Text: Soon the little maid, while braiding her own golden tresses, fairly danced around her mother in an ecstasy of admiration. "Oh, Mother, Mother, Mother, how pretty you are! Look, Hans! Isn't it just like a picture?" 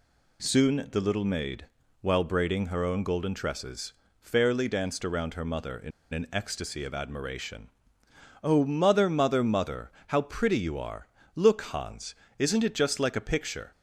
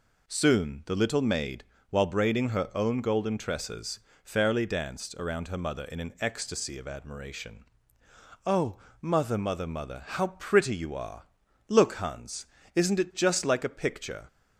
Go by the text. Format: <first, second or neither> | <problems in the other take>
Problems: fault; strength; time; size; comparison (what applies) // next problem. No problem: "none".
second | pauses between "in" and "an"; slight; at 5.9 s; 0.22 s long